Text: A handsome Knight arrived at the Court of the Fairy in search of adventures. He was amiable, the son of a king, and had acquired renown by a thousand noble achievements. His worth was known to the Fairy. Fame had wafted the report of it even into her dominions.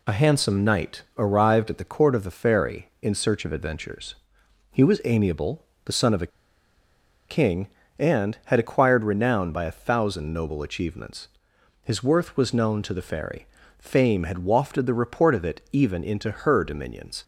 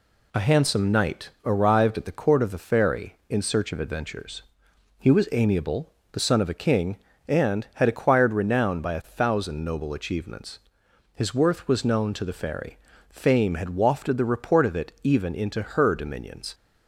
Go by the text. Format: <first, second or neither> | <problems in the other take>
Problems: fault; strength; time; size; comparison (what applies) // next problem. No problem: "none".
second | pauses between "a" and "king"; at 6.3 s; 1.0 s long